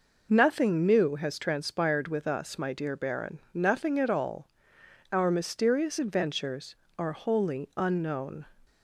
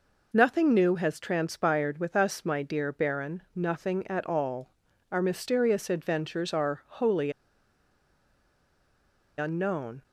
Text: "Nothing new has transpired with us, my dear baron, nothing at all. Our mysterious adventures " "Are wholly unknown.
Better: first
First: none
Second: pauses between "wholly" and "unknown"; strong; at 7.3 s; 2.0 s long

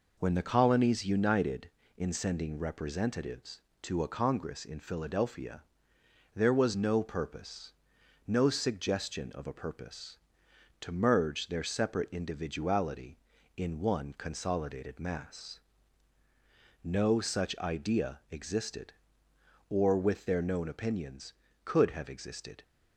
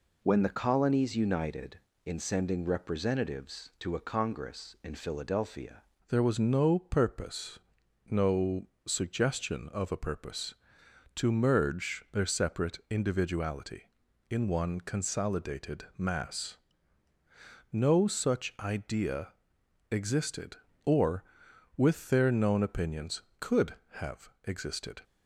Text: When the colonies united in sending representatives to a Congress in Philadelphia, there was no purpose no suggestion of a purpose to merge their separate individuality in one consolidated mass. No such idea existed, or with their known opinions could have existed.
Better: first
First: pauses between "purpose" and "no"; noticeable; at 7.7 s; 0.56 s long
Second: changes voice at "there"; from 6.0 s on; 19.0 s long // pauses between "purpose" and "no"; noticeable; at 7.5 s; 0.54 s long // pauses between "no" and "suggestion"; slight; at 8.6 s; 0.22 s long // pauses between "idea" and "existed"; noticeable; at 19.3 s; 0.60 s long // pauses between "have" and "existed"; slight; at 24.2 s; 0.16 s long

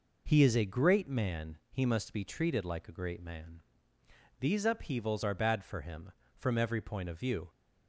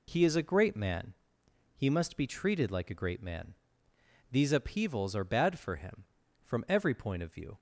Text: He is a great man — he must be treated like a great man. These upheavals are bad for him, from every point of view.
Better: neither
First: none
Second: none

